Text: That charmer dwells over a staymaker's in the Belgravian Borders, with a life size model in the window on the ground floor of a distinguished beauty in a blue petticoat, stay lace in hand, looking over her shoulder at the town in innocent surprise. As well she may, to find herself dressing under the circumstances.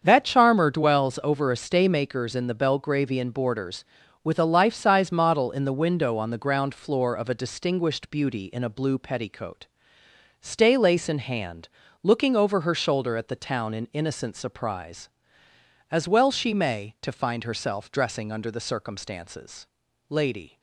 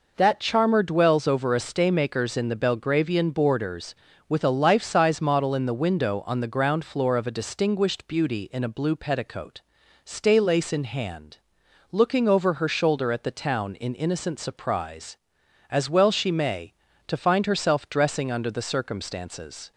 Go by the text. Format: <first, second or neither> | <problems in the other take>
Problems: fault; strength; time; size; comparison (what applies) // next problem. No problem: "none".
second | starts louder than the rest; strong; until 1.0 s; 7 dB // goes on to say "Lady"; from 20.0 s on; 0.50 s long